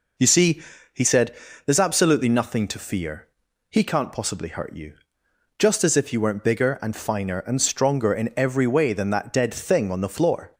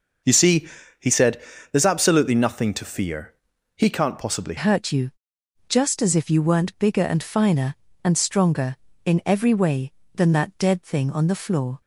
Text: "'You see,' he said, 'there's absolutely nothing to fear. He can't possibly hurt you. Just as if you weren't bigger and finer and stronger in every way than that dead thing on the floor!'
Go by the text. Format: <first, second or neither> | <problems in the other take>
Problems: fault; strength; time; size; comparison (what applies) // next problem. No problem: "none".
first | changes voice at "hurt"; from 4.5 s on; 7.3 s long